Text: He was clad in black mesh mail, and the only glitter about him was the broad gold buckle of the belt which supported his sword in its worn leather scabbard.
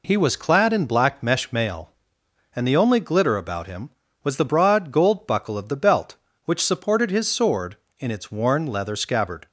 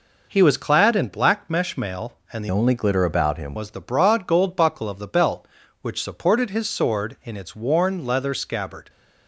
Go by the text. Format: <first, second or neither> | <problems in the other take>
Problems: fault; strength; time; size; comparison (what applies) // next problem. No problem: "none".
first | changes voice from "only" to "him"; from 2.5 to 3.5 s; 1.0 s long